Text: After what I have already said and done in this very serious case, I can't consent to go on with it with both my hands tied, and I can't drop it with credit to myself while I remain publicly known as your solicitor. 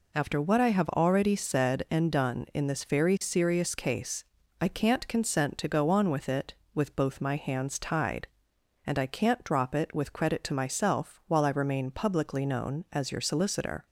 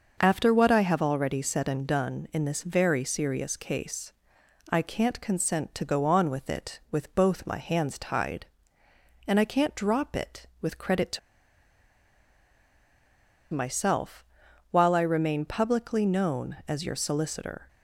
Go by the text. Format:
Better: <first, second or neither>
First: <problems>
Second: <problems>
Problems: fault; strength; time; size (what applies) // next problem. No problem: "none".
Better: first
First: none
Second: starts louder than the rest; until 1.2 s; 6 dB // pauses between "to" and "myself"; strong; at 11.1 s; 2.3 s long // pauses between "myself" and "while"; noticeable; at 14.2 s; 0.46 s long